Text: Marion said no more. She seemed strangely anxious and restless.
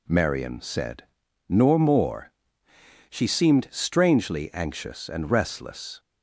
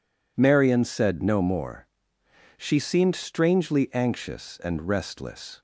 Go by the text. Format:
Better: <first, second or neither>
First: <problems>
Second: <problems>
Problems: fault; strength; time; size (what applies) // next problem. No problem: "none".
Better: second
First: says "nor" for "no"; at 1.4 s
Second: none